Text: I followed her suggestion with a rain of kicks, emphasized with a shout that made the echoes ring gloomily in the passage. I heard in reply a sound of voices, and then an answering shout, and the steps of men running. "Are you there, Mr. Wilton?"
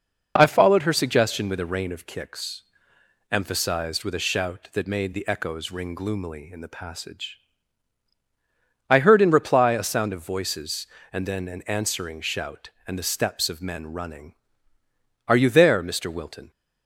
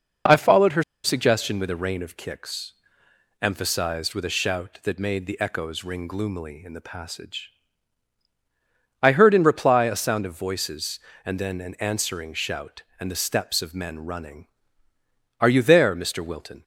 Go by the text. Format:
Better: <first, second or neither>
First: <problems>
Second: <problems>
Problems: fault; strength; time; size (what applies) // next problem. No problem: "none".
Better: first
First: none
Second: pauses between "her" and "suggestion"; slight; at 0.8 s; 0.21 s long